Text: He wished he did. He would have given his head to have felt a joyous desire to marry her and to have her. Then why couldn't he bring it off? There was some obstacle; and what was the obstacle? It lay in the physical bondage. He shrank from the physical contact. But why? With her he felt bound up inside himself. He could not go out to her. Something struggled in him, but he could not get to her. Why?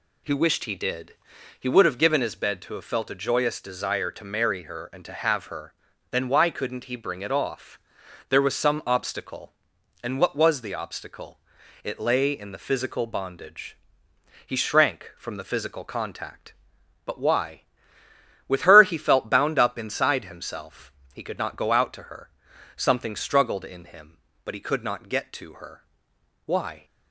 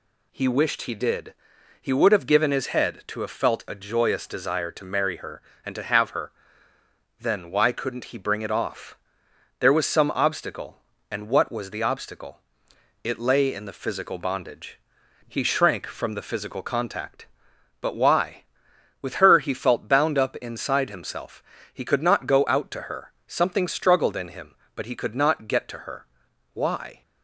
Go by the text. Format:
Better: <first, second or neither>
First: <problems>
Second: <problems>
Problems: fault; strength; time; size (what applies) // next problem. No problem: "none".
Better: second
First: says "bed" for "head"; at 2.3 s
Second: none